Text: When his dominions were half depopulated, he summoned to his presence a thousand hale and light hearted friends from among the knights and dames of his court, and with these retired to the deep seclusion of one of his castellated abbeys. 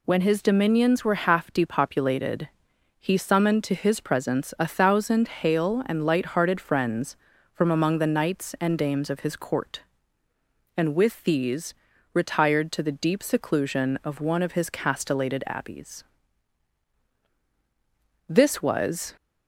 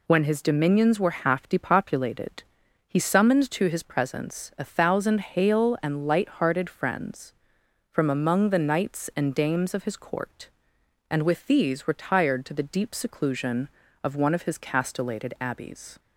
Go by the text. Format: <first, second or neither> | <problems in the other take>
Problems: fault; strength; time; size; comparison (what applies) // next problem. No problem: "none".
second | pauses between "these" and "retired"; at 11.7 s; 0.40 s long // goes on to say "This was"; noticeable; from 18.2 s on; 0.88 s long